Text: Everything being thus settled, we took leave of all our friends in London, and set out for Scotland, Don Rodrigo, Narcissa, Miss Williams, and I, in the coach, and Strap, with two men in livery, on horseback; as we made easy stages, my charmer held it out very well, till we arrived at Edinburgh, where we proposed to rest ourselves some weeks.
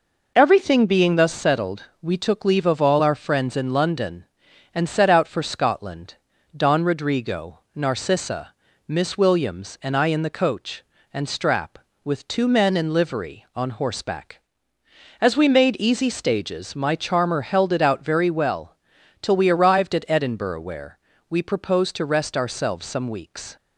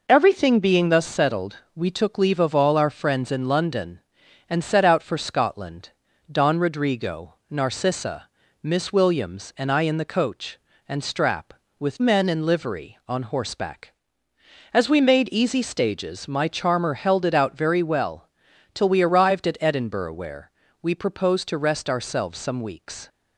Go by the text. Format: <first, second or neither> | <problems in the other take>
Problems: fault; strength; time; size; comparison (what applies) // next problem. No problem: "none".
first | skips "two"; at 12.0 s // pauses between "where" and "we"; slight; at 20.5 s; 0.32 s long; slight in the first